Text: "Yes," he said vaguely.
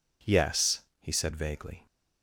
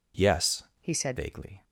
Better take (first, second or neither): first